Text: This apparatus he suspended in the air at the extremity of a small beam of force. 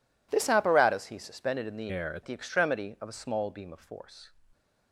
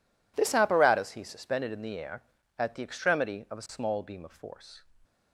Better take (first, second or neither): second